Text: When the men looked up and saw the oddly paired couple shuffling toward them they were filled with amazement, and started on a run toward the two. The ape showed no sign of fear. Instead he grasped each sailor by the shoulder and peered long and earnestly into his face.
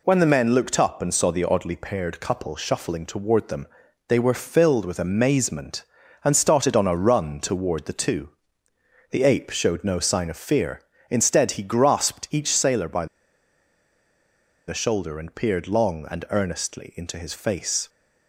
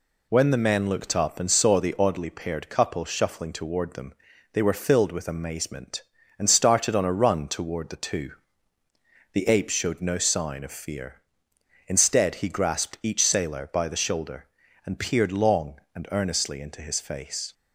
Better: second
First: pauses between "them" and "they"; at 3.6 s; 0.42 s long // pauses between "by" and "the"; strong; at 13.0 s; 1.6 s long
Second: pauses between "them" and "they"; at 4.1 s; 0.40 s long

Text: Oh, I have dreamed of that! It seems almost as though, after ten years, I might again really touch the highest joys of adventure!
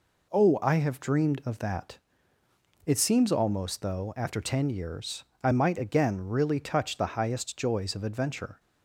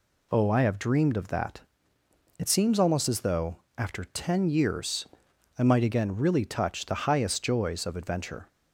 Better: second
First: skips "as"; at 3.8 s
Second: none

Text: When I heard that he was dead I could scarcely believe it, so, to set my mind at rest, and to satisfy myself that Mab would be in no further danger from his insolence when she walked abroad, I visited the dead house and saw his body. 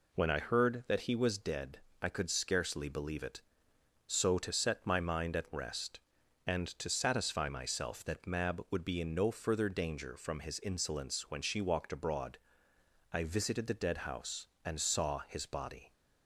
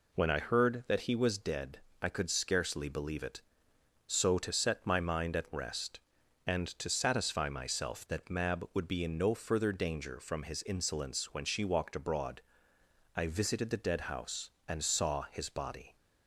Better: neither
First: pauses between "dead" and "I"; slight; at 1.7 s; 0.22 s long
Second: pauses between "dead" and "I"; slight; at 1.7 s; 0.22 s long

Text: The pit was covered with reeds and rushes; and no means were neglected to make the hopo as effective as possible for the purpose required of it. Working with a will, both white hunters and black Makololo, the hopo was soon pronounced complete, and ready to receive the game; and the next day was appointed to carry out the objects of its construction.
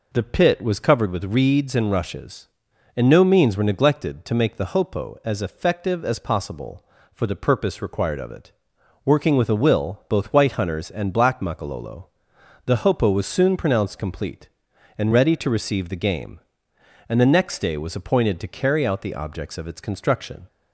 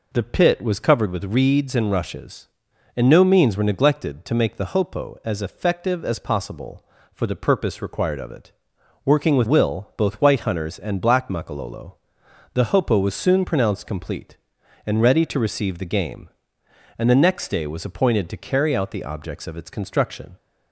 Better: first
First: none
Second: skips "a"; at 9.4 s

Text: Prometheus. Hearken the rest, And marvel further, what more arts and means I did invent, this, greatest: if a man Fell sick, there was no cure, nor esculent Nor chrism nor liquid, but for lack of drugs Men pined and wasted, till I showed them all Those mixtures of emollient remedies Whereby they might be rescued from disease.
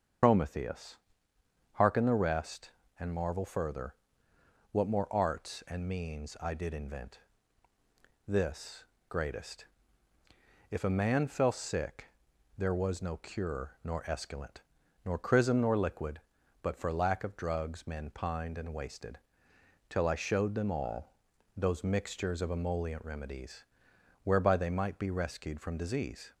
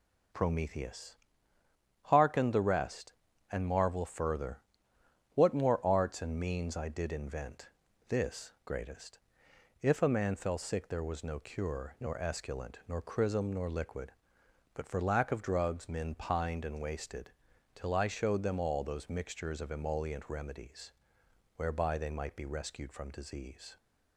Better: second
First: loses the start of "Prometheus"; at 0.2 s; 80 ms // starts louder than the rest; until 1.9 s; 7 dB // pauses between "esculent" and "Nor"; at 14.6 s; 0.42 s long // pauses between "all" and "Those"; at 21.1 s; 0.42 s long // pauses between "remedies" and "Whereby"; noticeable; at 23.6 s; 0.62 s long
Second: pauses between "remedies" and "Whereby"; noticeable; at 20.9 s; 0.64 s long

